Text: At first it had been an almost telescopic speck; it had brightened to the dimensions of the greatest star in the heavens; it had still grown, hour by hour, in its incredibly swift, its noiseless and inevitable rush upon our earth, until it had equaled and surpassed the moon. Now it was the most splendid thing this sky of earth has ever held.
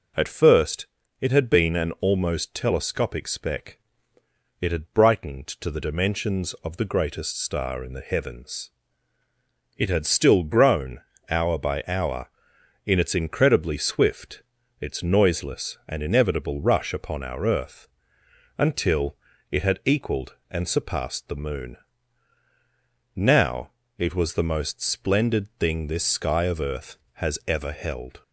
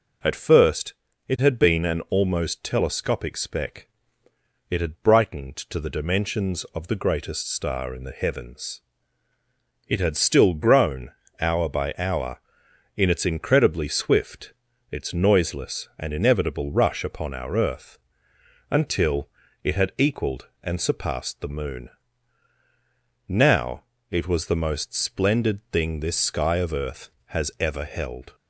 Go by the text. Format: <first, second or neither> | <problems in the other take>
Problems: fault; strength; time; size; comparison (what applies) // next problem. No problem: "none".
neither | pauses between "first" and "it"; slight; the same in both // pauses between "until" and "it"; slight; the same in both // pauses between "Now" and "it"; slight; the same in both